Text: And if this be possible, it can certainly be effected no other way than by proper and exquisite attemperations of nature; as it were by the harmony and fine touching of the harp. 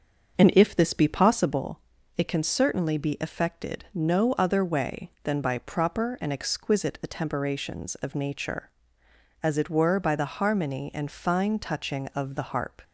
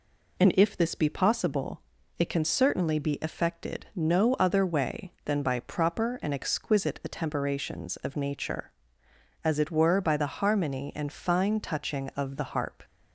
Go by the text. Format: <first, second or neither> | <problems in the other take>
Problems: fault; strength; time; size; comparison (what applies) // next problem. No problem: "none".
second | starts louder than the rest; until 1.7 s; 6.5 dB